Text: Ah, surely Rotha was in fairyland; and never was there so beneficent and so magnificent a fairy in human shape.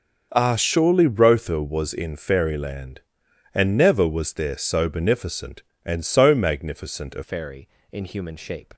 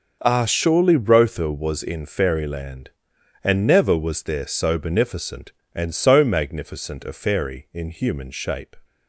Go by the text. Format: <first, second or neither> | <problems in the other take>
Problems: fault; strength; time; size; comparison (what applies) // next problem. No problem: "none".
second | changes voice at "fairy"; from 7.2 s on; 1.5 s long